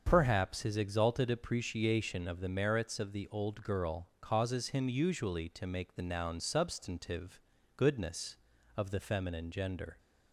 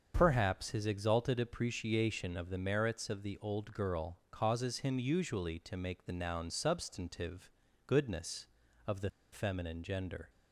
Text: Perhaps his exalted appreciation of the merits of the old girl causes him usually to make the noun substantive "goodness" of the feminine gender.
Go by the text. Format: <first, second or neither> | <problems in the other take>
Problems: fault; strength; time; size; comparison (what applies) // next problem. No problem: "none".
first | starts louder than the rest; until 1.1 s; 7 dB; also in the first // pauses between "substantive" and "goodness"; slight; at 7.4 s; 0.36 s long; slight in the first // pauses between "the" and "feminine"; slight; at 9.0 s; 0.22 s long